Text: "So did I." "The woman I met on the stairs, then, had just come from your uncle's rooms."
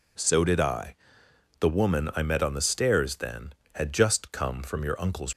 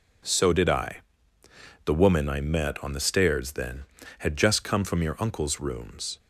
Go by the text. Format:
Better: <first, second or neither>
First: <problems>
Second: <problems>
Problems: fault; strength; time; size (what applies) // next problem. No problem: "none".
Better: second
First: stops before "rooms"; at 5.3 s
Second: none